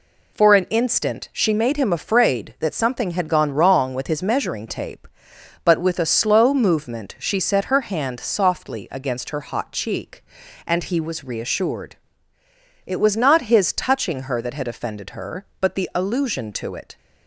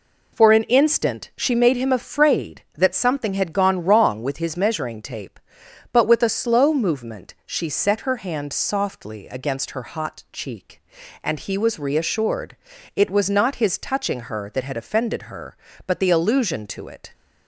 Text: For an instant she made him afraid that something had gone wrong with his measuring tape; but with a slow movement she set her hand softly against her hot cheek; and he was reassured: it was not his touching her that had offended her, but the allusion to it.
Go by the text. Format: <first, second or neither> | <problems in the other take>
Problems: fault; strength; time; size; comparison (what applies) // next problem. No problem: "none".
neither | none